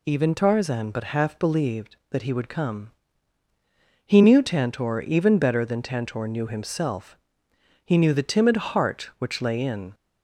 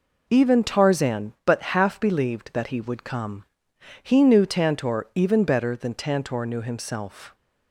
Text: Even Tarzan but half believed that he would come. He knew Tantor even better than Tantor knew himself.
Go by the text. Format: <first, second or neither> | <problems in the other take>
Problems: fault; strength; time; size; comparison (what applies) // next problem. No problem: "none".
second | goes on to say "He knew the timid heart which lay in"; strong; from 7.8 s on; 2.0 s long